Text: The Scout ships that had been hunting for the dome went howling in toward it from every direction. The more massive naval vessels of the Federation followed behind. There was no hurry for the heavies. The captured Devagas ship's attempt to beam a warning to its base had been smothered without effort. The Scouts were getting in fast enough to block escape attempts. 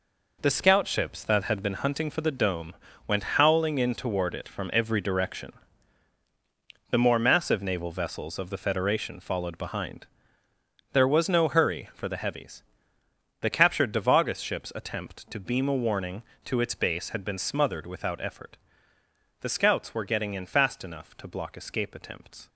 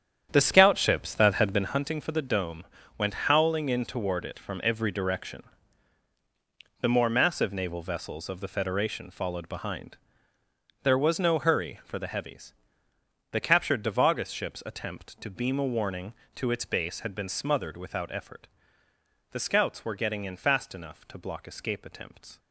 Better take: first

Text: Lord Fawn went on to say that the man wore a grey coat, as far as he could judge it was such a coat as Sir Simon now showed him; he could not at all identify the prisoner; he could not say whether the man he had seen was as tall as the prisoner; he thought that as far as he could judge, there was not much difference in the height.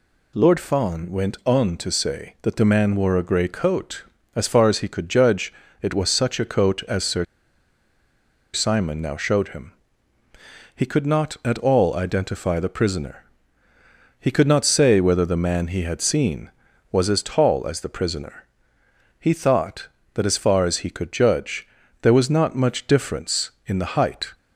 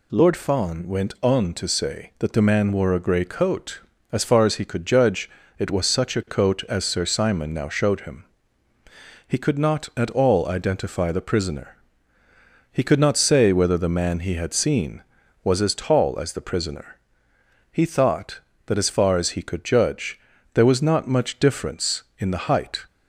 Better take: second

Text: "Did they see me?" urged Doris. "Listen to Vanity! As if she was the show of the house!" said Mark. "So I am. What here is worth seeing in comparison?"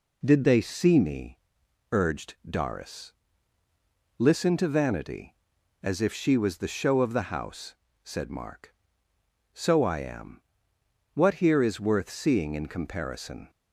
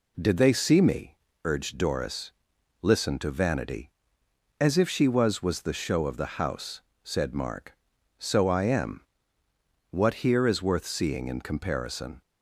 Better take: first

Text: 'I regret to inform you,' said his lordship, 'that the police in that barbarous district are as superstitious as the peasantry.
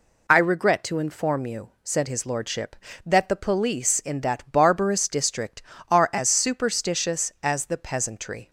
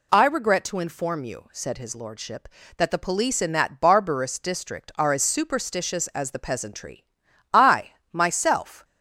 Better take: first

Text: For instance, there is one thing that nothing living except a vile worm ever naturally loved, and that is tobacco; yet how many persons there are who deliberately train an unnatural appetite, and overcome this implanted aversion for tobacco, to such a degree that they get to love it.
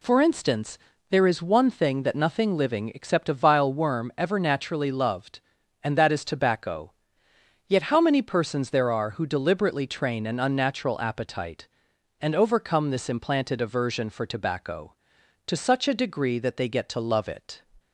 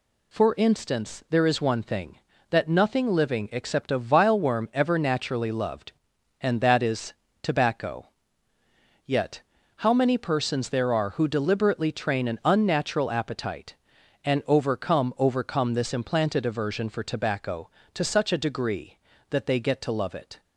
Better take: first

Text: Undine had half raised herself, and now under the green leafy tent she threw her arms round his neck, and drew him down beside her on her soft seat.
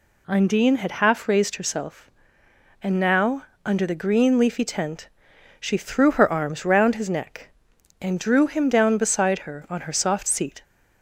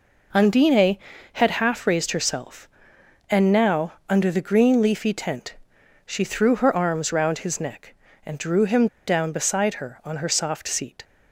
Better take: first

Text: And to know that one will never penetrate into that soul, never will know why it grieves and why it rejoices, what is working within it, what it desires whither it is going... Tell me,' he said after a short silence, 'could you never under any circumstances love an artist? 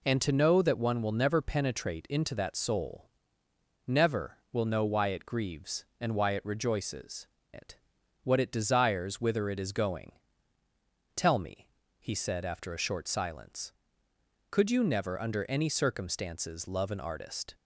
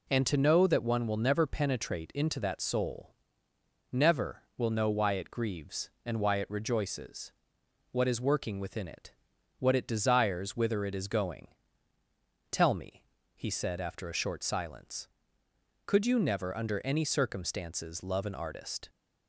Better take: second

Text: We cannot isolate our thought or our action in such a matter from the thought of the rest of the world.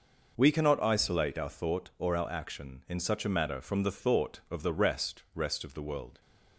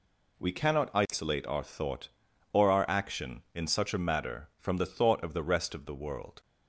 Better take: second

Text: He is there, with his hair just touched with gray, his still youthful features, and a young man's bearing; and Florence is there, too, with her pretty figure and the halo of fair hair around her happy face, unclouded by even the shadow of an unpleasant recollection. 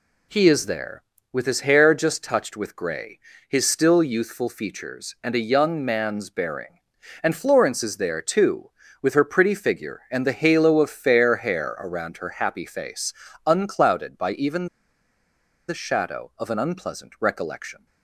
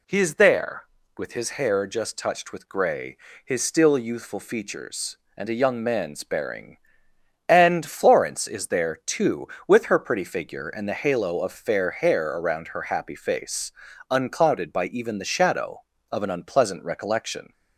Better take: second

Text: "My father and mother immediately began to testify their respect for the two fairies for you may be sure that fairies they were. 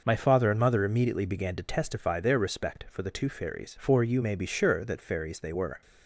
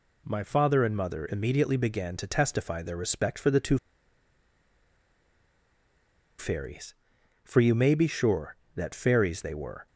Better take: first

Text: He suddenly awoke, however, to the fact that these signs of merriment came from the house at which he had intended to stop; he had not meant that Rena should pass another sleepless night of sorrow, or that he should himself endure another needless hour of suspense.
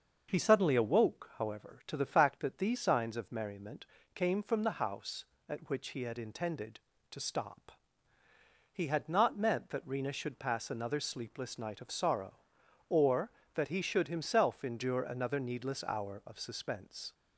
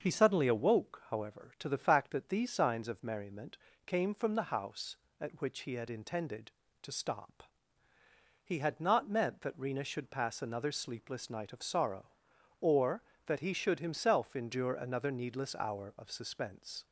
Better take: neither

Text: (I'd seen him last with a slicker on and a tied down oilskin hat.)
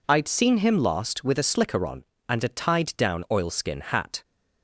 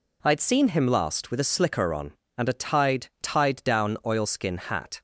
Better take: first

